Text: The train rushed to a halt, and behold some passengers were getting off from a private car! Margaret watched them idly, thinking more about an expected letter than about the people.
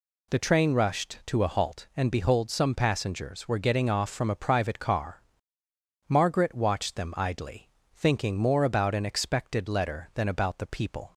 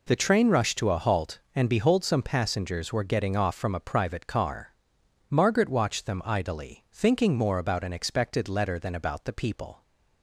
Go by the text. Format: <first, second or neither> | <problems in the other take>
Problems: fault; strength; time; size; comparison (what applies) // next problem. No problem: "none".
neither | none